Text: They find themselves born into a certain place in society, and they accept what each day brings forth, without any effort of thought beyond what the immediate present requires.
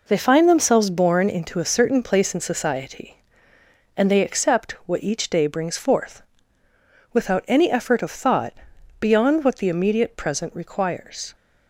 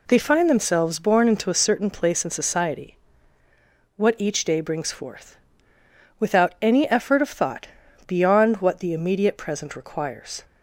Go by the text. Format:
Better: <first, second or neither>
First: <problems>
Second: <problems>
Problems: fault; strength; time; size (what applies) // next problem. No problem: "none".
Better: first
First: pauses between "thought" and "beyond"; noticeable; at 8.5 s; 0.46 s long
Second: skips "and they accept"; at 3.4 s // pauses between "thought" and "beyond"; at 7.6 s; 0.40 s long